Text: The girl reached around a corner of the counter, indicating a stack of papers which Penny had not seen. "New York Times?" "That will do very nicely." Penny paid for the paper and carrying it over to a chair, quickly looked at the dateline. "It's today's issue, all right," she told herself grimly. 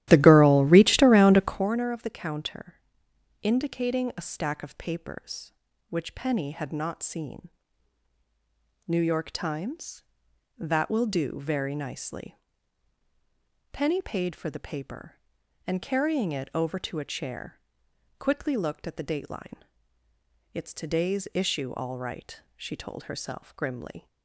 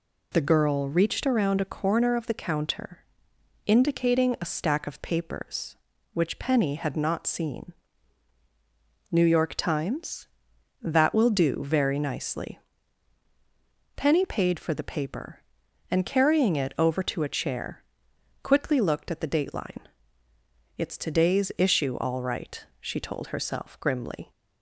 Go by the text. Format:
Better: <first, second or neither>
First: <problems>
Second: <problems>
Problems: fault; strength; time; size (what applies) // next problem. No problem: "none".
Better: second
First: starts louder than the rest; strong; until 1.7 s; 13.5 dB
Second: none